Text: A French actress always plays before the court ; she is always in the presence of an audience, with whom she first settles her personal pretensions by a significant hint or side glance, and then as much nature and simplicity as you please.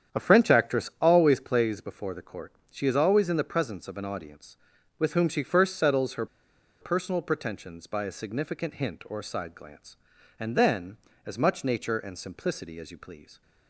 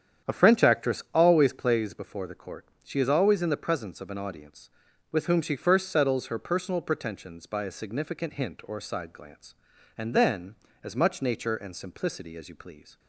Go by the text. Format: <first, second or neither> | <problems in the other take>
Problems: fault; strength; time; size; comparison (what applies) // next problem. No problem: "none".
second | starts louder than the rest; strong; until 1.2 s; 9 dB; strong in the second // pauses between "her" and "personal"; noticeable; at 6.2 s; 0.55 s long